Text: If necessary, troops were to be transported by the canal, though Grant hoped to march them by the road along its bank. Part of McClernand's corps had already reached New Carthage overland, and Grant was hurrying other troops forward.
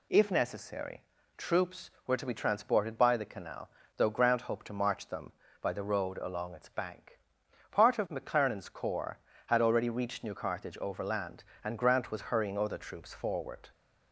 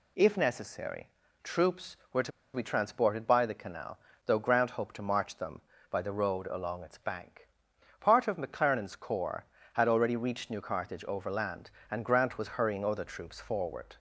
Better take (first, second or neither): first